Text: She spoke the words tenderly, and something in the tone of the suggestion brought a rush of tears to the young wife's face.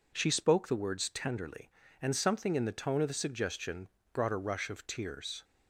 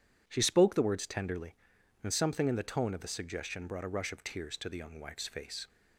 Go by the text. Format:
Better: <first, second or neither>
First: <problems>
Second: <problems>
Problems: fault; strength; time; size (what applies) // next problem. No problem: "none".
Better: second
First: pauses between "suggestion" and "brought"; slight; at 3.8 s; 0.26 s long // stops before "to the young wife's face"; at 5.4 s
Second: none